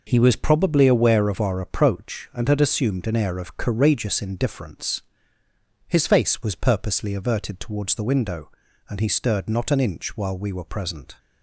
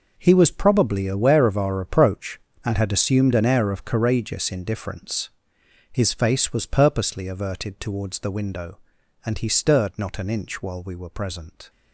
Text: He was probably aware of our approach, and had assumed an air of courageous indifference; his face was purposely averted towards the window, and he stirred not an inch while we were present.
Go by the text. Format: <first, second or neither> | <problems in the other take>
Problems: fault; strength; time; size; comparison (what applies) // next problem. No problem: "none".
first | gets quieter; strong; throughout; 12.5 dB